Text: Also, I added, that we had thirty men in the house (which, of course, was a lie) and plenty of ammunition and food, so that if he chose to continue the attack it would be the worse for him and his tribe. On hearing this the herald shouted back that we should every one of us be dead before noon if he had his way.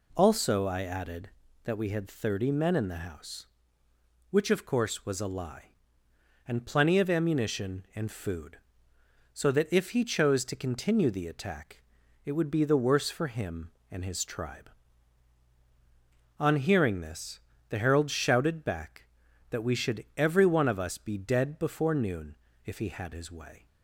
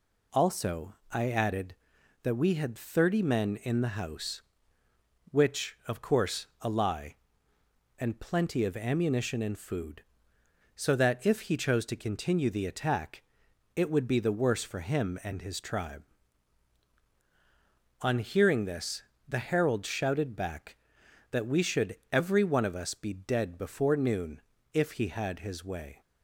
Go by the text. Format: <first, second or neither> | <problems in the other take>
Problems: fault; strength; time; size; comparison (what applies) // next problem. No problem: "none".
first | skips "was"; at 6.5 s // pauses between "attack" and "it"; noticeable; at 13.2 s; 0.52 s long; also in the first // pauses between "this" and "the"; slight; at 19.0 s; 0.26 s long; slight in the first // pauses between "should" and "every"; slight; at 21.9 s; 0.18 s long // pauses between "noon" and "if"; slight; at 24.4 s; 0.32 s long; slight in the first